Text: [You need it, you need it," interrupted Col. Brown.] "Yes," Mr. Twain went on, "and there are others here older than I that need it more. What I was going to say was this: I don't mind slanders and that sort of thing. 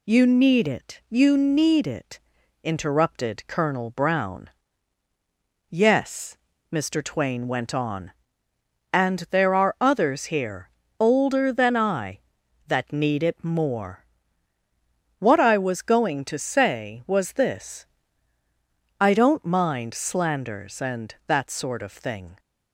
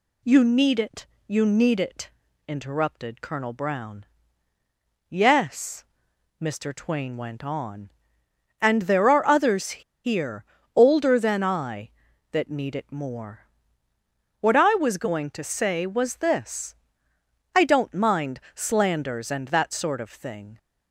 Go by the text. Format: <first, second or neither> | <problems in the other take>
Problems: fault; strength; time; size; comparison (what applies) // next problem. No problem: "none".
first | pauses between "others" and "here"; slight; at 9.8 s; 0.21 s long // pauses between "here" and "older"; slight; at 10.4 s; 0.32 s long; slight in the first